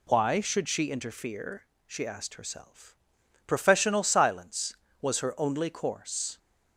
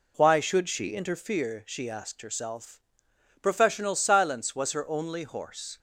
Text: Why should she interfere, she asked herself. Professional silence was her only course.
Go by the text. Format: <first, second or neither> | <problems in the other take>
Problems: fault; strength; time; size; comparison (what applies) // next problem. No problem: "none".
first | says "horse" for "course"; at 5.2 s